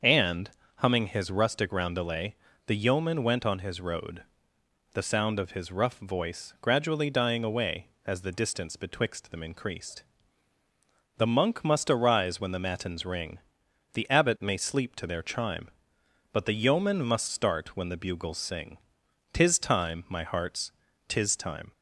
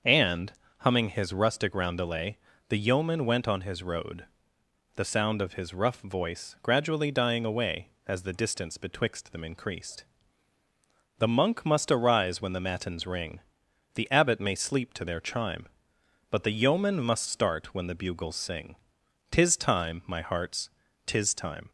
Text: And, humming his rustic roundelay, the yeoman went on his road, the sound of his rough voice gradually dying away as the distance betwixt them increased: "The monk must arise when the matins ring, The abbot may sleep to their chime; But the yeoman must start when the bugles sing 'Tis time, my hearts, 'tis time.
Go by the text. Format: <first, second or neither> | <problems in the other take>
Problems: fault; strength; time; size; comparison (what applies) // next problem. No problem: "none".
neither | starts louder than the rest; the same in both // pauses between "sing" and "Tis"; noticeable; the same in both